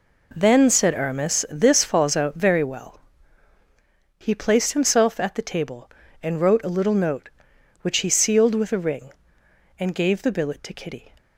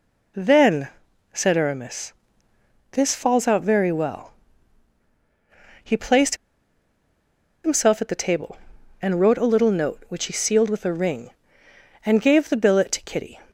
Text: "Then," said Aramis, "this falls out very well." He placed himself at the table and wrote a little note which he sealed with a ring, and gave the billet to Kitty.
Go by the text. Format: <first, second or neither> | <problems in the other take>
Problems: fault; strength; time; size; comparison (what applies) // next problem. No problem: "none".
first | pauses between "placed" and "himself"; strong; at 6.3 s; 1.2 s long